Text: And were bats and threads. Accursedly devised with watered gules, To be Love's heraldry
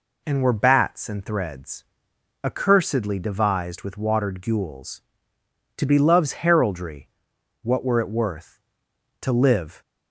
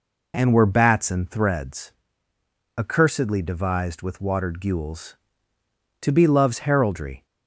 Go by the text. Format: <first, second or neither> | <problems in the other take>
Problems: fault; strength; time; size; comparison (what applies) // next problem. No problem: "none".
second | goes on to say "What were it worth To live"; strong; from 7.6 s on; 2.2 s long